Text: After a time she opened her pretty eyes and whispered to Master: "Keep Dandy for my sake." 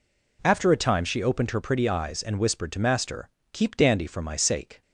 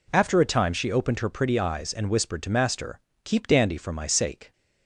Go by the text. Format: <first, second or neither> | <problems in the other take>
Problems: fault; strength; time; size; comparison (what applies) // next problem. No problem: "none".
neither | none